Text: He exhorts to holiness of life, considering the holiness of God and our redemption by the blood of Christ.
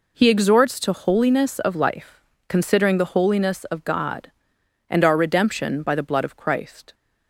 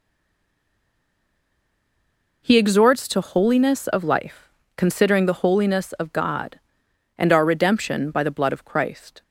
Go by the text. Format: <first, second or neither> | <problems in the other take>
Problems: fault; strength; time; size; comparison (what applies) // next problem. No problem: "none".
first | stays silent before the first word; until 2.4 s; 2.4 s long